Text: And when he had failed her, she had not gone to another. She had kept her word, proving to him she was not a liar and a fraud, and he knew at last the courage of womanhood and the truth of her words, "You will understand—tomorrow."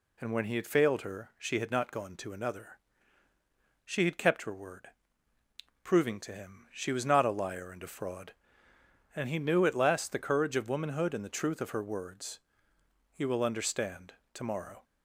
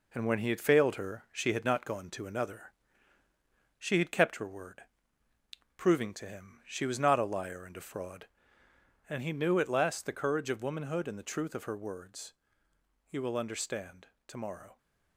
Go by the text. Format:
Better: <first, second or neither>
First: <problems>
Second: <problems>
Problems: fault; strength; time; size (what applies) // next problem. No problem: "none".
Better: first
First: none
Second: gets quieter; noticeable; throughout; 5.5 dB